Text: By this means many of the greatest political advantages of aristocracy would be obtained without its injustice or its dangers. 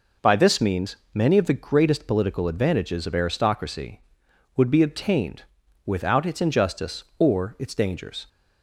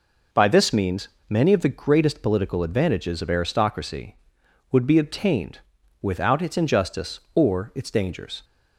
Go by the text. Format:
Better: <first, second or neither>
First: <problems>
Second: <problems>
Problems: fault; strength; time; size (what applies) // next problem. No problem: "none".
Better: neither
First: pauses between "means" and "many"; slight; at 0.9 s; 0.18 s long // pauses between "obtained" and "without"; at 5.4 s; 0.42 s long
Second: pauses between "means" and "many"; slight; at 1.0 s; 0.21 s long // pauses between "obtained" and "without"; at 5.5 s; 0.42 s long